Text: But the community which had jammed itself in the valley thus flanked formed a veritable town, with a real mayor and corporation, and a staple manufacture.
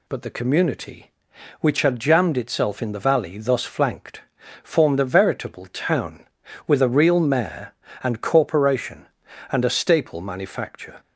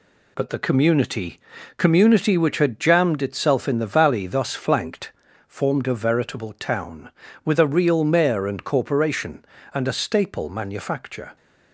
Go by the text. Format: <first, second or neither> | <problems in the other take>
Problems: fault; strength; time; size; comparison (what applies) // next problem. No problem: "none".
first | says "community" twice; at 1.7 s // pauses between "flanked" and "formed"; slight; at 5.1 s; 0.36 s long; also in the first